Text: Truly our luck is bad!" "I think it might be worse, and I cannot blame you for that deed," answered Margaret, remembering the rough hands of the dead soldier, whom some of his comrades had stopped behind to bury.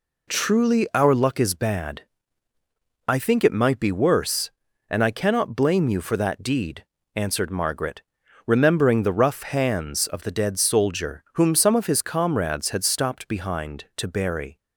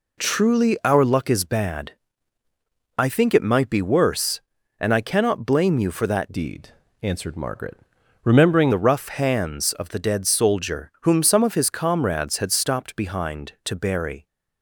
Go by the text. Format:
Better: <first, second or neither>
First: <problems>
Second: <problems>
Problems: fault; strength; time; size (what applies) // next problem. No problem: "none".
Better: first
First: none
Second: changes voice from "deed" to "remembering"; from 6.3 to 8.7 s; 2.4 s long